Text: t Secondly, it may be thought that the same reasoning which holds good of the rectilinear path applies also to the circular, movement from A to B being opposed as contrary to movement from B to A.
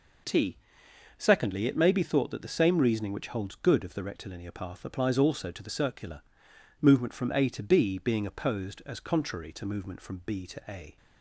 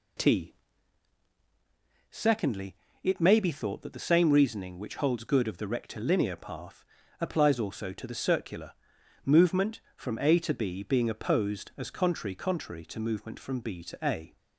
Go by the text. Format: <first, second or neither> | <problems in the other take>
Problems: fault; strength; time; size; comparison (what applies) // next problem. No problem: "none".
first | pauses between "t" and "Secondly"; strong; at 0.5 s; 1.5 s long; noticeable in the first // pauses between "path" and "applies"; at 6.8 s; 0.36 s long // says "contrary" twice; at 12.3 s